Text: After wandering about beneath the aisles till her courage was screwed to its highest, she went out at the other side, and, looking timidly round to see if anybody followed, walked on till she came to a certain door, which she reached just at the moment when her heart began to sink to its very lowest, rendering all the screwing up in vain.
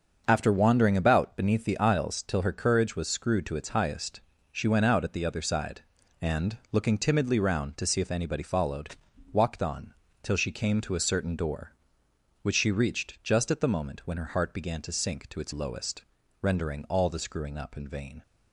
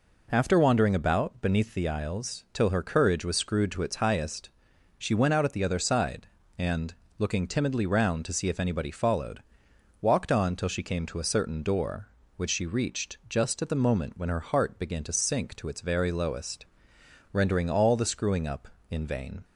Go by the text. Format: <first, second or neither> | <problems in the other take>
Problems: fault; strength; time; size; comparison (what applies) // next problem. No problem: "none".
second | starts louder than the rest; until 1.2 s; 6.5 dB // pauses between "on" and "till"; slight; at 9.9 s; 0.30 s long // skips "very"; at 15.5 s